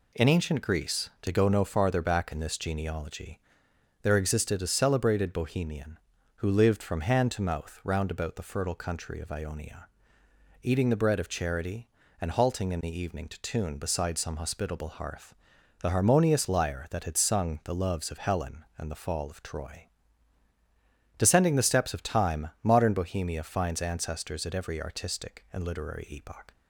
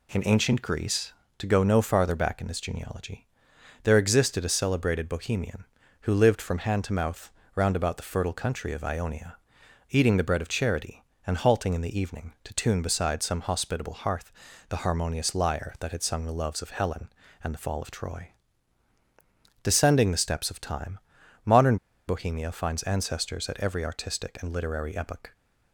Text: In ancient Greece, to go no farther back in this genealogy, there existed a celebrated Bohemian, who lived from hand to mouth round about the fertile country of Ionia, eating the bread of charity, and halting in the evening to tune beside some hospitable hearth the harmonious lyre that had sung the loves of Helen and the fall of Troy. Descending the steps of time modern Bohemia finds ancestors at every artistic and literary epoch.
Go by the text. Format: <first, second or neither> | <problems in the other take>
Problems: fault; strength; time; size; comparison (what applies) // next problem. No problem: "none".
first | pauses between "mouth" and "round"; slight; at 7.2 s; 0.24 s long // pauses between "hearth" and "the"; slight; at 14.3 s; 0.36 s long; noticeable in the first // pauses between "time" and "modern"; noticeable; at 20.9 s; 0.46 s long // pauses between "modern" and "Bohemia"; slight; at 21.7 s; 0.31 s long